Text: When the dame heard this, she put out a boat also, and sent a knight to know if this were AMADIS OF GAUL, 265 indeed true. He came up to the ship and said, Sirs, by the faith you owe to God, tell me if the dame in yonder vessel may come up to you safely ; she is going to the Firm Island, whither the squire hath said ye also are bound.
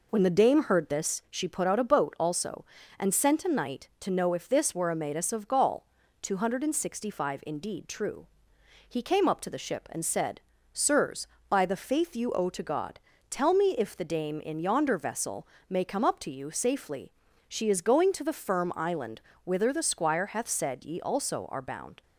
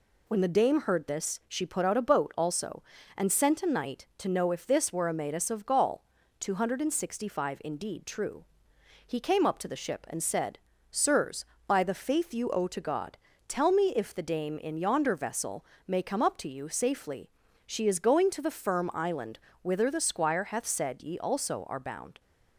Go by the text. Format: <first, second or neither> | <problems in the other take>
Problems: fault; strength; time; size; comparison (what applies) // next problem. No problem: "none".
second | starts louder than the rest; noticeable; until 1.3 s; 4.5 dB // pauses between "vessel" and "may"; slight; at 15.4 s; 0.22 s long; slight in the second